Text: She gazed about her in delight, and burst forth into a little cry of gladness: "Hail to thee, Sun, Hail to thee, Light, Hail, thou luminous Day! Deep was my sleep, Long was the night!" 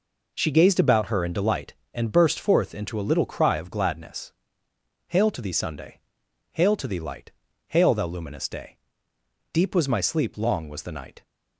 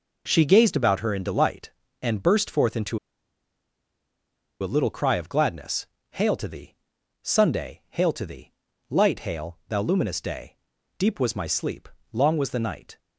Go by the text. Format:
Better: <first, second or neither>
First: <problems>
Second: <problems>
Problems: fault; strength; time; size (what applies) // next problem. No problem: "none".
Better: first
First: none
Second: pauses between "into" and "a"; strong; at 2.9 s; 1.6 s long